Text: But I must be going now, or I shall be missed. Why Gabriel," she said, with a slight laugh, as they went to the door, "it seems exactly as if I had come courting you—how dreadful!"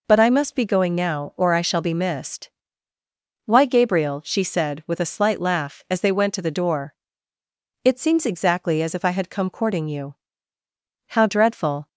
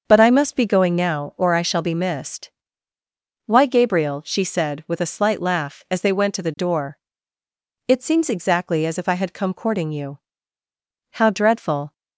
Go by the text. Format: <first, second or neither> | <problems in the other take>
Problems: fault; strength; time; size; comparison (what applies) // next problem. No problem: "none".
first | starts louder than the rest; until 1.3 s; 6.5 dB